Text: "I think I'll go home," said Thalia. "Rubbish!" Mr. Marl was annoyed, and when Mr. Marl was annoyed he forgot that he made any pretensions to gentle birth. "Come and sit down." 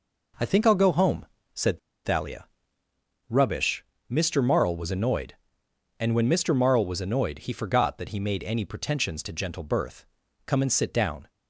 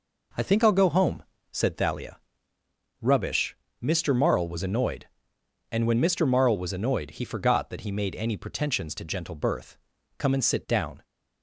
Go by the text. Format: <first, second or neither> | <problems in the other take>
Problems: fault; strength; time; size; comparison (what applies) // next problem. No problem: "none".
second | pauses between "said" and "Thalia"; slight; at 1.7 s; 0.26 s long